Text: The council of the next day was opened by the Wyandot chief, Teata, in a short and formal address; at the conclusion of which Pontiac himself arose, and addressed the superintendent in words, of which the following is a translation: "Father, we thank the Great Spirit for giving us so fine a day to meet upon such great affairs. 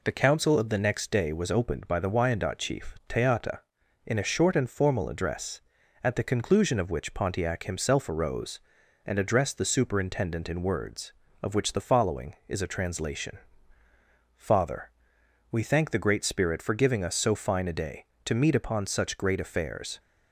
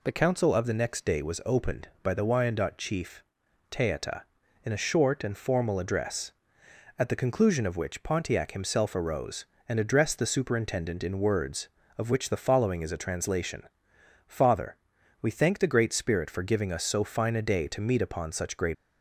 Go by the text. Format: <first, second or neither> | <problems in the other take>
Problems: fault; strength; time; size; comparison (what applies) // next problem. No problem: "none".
first | stops before "affairs"; at 18.7 s